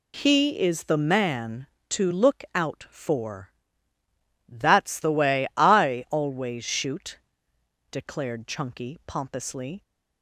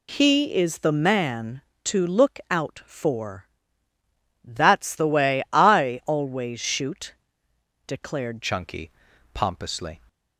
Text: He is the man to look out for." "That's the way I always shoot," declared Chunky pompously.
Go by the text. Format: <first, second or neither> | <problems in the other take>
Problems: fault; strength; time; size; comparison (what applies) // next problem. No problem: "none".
first | changes voice at "Chunky"; from 8.4 s on; 1.6 s long // pauses between "Chunky" and "pompously"; at 8.9 s; 0.42 s long